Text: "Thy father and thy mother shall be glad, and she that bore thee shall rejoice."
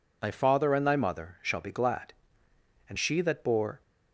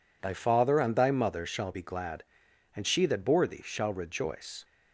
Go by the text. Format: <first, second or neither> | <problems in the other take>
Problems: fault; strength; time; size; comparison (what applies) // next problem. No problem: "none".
second | stops before "thee shall rejoice"; at 3.8 s